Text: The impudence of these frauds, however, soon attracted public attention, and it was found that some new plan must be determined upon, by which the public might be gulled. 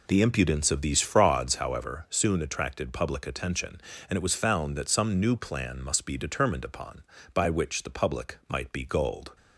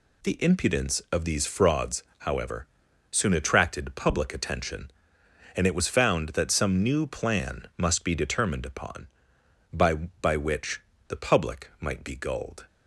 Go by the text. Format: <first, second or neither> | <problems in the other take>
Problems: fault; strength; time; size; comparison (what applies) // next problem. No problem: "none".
first | says "by" twice; at 10.2 s // pauses between "which" and "the"; slight; at 10.8 s; 0.26 s long